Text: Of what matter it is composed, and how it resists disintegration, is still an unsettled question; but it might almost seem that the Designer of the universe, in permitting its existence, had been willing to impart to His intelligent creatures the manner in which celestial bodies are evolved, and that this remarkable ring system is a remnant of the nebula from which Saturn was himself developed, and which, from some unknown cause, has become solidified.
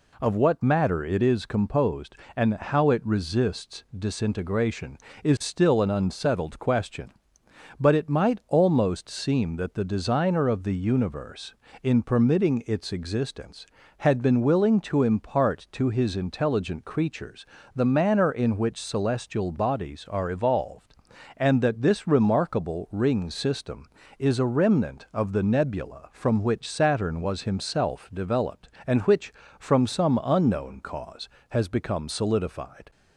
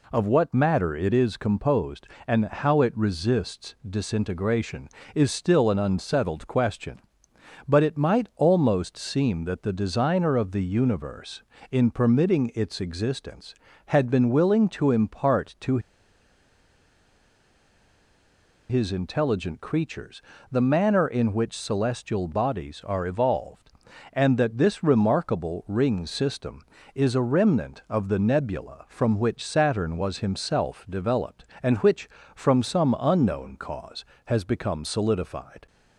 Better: first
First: pauses between "creatures" and "the"; slight; at 17.4 s; 0.30 s long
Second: pauses between "to" and "His"; strong; at 15.7 s; 2.9 s long // pauses between "creatures" and "the"; slight; at 20.2 s; 0.30 s long

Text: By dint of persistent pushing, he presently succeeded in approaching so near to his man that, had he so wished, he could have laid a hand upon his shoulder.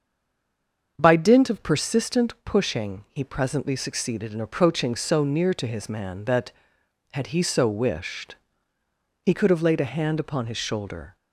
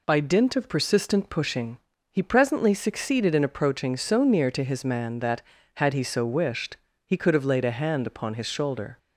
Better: second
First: stays silent before the first word; until 0.9 s; 0.9 s long // starts louder than the rest; until 1.9 s; 7 dB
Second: none

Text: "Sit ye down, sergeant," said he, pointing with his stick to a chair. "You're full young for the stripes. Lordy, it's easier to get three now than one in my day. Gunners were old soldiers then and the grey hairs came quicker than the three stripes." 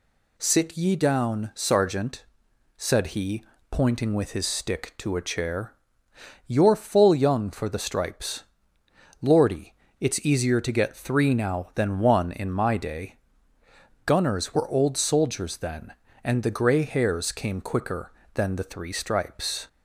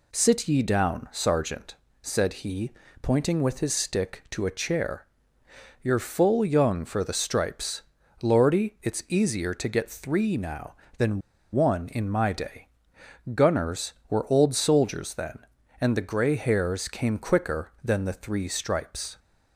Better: first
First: none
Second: pauses between "than" and "one"; slight; at 11.2 s; 0.31 s long

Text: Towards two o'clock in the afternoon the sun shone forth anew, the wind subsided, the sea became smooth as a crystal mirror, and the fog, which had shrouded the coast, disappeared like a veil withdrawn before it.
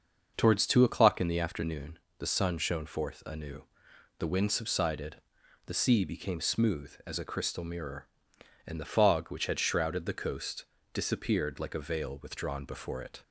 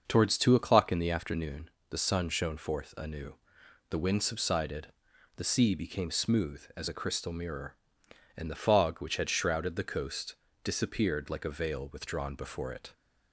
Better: neither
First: starts louder than the rest; until 1.3 s; 6 dB // pauses between "afternoon" and "the"; slight; at 1.9 s; 0.20 s long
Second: starts louder than the rest; until 1.0 s; 6 dB // pauses between "afternoon" and "the"; slight; at 1.6 s; 0.20 s long

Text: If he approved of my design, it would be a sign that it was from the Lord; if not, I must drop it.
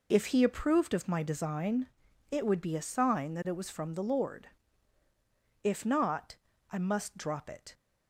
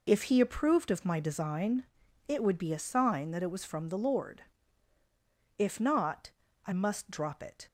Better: neither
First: none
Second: none

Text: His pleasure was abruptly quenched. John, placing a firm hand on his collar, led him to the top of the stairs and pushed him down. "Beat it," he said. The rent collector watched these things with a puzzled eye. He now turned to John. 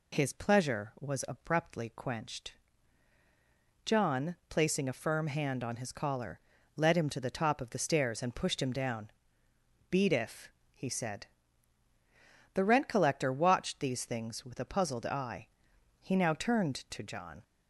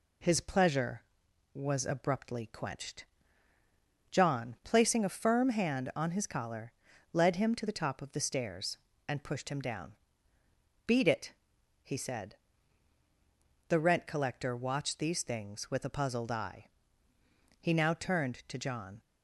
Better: second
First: says "if" for "it"; at 10.1 s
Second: none

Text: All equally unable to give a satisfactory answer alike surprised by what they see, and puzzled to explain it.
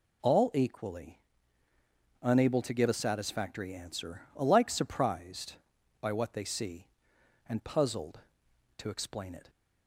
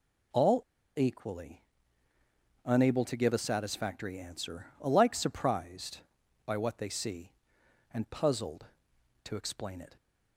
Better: first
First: pauses between "equally" and "unable"; at 1.1 s; 1.0 s long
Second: pauses between "All" and "equally"; at 0.6 s; 0.36 s long // pauses between "equally" and "unable"; at 1.6 s; 1.0 s long

